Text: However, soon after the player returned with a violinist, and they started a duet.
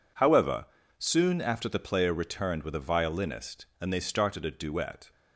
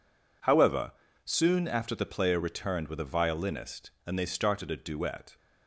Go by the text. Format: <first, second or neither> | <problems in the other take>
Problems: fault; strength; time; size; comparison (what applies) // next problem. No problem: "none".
neither | none